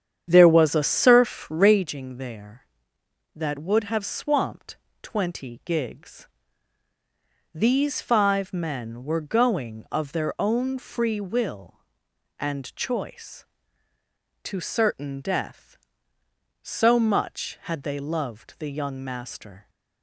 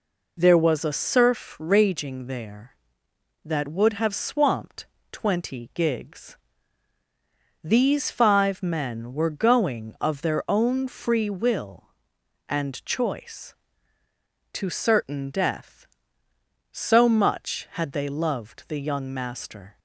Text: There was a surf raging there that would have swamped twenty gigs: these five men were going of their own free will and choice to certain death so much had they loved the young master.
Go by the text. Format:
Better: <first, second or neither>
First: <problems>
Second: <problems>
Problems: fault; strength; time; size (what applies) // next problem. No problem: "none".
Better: second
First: starts louder than the rest; strong; until 1.9 s; 8.5 dB // pauses between "swamped" and "twenty"; slight; at 4.7 s; 0.24 s long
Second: pauses between "swamped" and "twenty"; slight; at 4.8 s; 0.24 s long